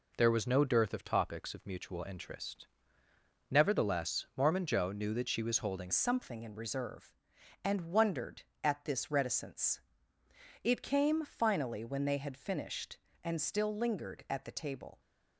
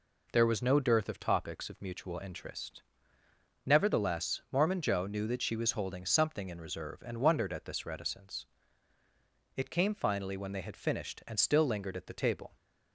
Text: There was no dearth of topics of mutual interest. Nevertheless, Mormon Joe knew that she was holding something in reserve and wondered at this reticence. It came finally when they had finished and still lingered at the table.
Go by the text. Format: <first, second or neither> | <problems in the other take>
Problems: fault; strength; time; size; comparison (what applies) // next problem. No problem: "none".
second | changes voice at "something"; from 5.9 s on; 9.1 s long